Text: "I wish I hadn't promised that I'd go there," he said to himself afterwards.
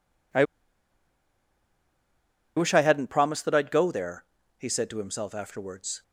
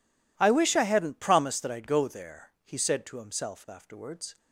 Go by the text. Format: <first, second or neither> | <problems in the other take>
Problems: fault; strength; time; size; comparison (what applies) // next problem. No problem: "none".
second | pauses between "I" and "wish"; strong; at 0.4 s; 2.1 s long